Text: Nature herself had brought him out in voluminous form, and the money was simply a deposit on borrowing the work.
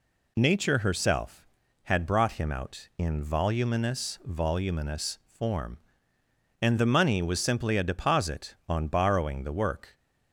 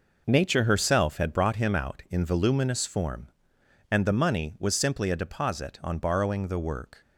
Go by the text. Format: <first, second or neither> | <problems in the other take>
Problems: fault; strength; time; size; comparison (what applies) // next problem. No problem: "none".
second | says "voluminous" twice; at 4.2 s